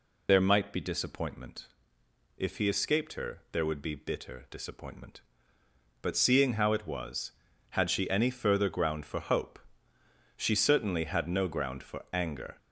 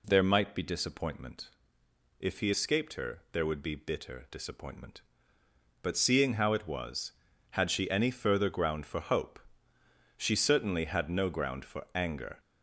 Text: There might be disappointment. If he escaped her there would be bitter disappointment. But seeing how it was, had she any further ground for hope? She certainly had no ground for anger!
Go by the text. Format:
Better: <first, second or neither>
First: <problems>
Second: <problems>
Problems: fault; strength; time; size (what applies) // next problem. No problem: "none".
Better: second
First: loses the start of "There"; at 0.2 s; 75 ms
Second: none